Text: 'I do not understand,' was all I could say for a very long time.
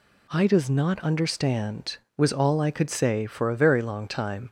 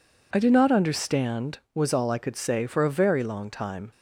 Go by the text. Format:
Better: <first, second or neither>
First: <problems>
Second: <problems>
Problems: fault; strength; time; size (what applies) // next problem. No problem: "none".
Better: second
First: says "does" for "do"; at 0.4 s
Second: none